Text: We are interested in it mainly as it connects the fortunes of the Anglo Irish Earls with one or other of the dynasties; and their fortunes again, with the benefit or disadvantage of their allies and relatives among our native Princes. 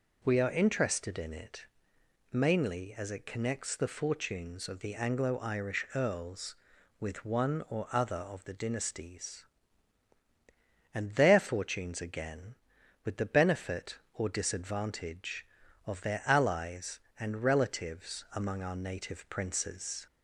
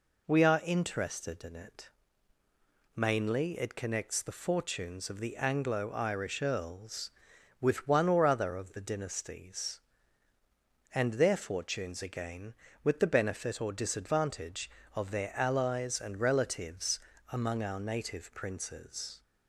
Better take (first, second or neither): first